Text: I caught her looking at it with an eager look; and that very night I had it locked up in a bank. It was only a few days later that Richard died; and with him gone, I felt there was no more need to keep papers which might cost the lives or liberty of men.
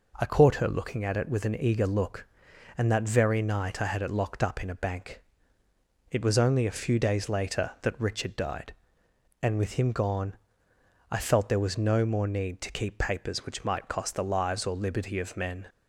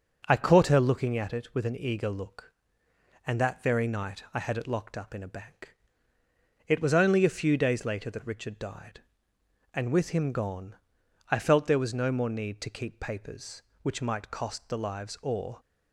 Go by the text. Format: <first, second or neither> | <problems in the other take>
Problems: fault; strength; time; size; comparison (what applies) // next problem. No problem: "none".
first | starts louder than the rest; until 1.2 s; 7 dB // stops before "liberty of men"; at 15.5 s